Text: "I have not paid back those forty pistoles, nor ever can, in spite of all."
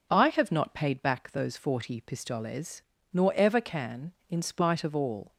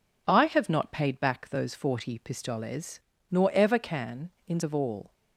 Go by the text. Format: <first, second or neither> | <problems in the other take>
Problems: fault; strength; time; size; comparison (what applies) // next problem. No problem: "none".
first | skips "spite"; at 4.6 s